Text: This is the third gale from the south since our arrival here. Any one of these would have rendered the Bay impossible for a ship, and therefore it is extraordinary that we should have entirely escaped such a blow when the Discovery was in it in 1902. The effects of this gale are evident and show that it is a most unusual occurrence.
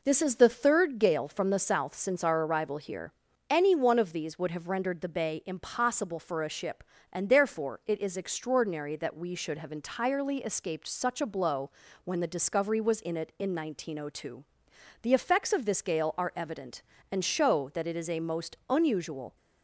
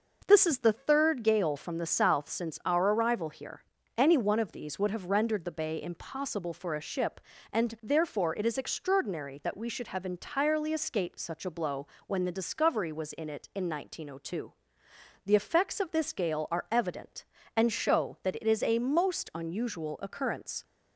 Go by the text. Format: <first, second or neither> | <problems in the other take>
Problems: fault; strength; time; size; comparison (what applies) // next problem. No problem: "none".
second | pauses between "blow" and "when"; slight; at 11.6 s; 0.34 s long; slight in the second // stops before "occurrence"; at 19.3 s